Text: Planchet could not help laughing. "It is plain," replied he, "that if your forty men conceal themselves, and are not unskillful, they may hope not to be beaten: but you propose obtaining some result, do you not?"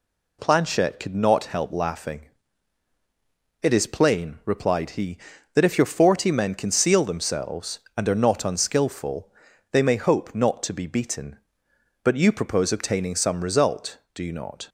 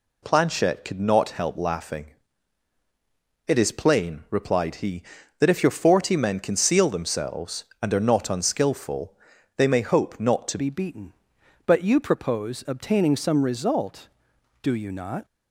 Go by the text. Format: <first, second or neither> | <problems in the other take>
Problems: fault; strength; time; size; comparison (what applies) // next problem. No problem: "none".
first | changes voice at "be"; from 10.5 s on; 4.7 s long